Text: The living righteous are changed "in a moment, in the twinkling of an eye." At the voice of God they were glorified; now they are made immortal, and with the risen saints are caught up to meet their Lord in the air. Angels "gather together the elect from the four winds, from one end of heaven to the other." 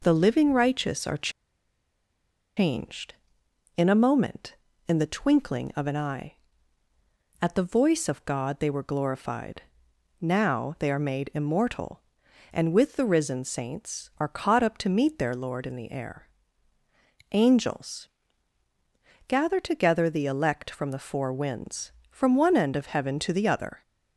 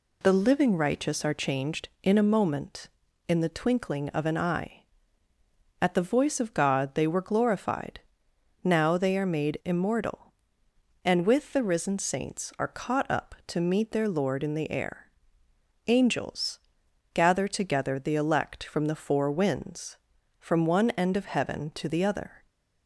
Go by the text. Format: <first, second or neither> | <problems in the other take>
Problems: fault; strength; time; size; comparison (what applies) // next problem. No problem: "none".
second | pauses between "are" and "changed"; strong; at 1.2 s; 1.2 s long // pauses between "Angels" and "gather"; at 18.0 s; 1.2 s long; noticeable in the second